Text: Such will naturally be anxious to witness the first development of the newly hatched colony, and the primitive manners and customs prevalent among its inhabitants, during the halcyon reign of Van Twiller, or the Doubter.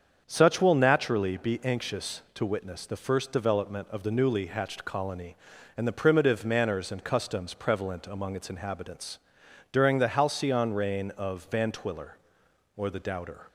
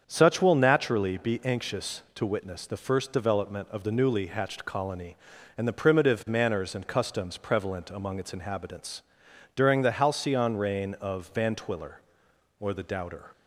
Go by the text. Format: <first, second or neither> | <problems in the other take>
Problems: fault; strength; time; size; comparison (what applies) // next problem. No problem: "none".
neither | starts louder than the rest; strong; the same in both